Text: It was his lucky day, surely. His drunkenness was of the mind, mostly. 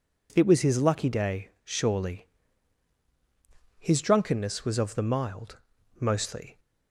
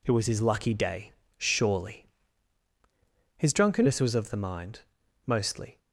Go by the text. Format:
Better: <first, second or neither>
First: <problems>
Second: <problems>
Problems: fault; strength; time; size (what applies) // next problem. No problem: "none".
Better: second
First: says "mild" for "mind"; at 5.0 s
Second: none